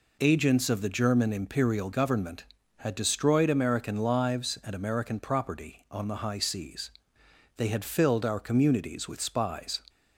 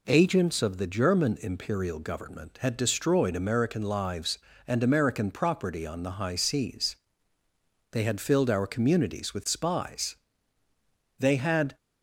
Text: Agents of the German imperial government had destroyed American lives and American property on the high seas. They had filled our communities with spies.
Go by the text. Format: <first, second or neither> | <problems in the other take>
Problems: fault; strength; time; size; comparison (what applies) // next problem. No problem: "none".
first | goes on to say "They had"; from 11.1 s on; 0.58 s long